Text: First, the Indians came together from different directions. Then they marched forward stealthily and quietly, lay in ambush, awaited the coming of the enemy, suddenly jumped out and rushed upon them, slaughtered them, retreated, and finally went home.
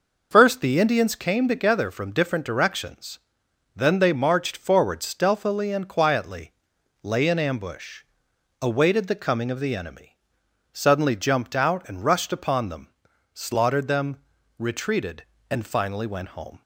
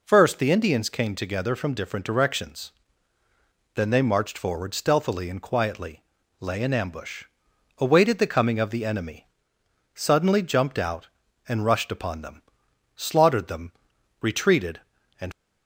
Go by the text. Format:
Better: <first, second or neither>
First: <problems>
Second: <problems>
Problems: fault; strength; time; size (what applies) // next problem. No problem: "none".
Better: first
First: none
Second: stops before "finally went home"; at 15.3 s